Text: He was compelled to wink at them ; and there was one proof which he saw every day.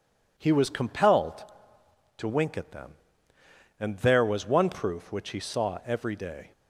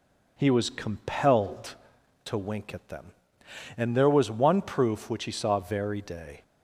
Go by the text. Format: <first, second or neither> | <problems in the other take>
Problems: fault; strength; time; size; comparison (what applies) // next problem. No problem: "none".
first | says "very" for "every"; at 5.5 s